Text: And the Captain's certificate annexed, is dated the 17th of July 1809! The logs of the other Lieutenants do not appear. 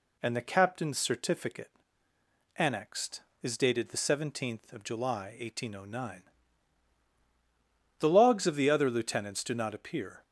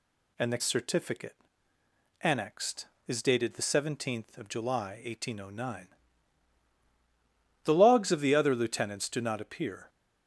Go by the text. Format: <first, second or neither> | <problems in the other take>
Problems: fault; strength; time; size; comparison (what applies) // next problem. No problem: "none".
first | skips "Captain's"; at 0.6 s // pauses between "certificate" and "annexed"; noticeable; at 1.3 s; 0.88 s long; noticeable in the first